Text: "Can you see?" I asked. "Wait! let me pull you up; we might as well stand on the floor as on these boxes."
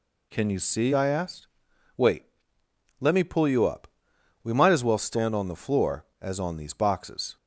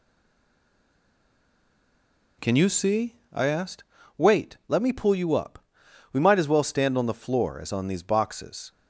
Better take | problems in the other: first | stays silent before the first word; until 2.3 s; 2.3 s long

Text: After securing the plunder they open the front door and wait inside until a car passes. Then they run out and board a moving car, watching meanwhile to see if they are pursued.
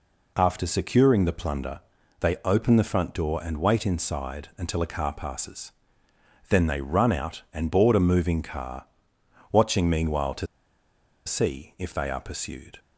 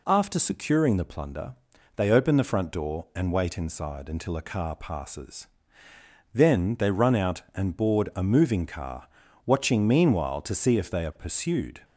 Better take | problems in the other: second | pauses between "plunder" and "they"; at 1.7 s; 0.42 s long; also in the second // pauses between "to" and "see"; noticeable; at 10.4 s; 0.80 s long

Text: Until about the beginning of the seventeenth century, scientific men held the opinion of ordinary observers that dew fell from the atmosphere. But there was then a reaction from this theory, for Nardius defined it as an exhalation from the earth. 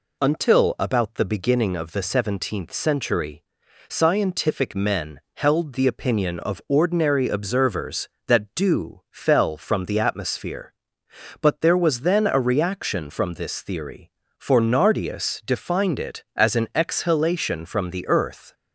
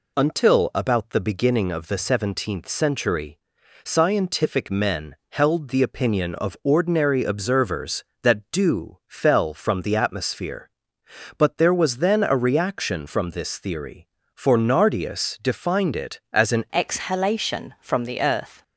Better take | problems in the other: first | pauses between "men" and "held"; slight; at 5.1 s; 0.16 s long; slight in the first // changes voice at "exhalation"; from 16.7 s on; 1.9 s long

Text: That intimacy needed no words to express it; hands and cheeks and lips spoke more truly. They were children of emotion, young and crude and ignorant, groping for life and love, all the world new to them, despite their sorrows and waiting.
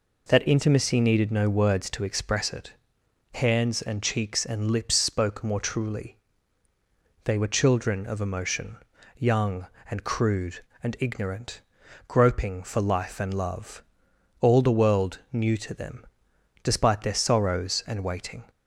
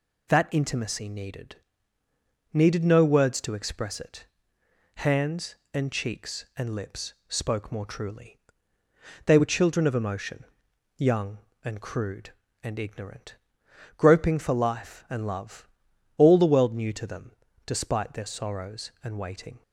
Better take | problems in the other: first | says "needed" twice; at 2.5 s

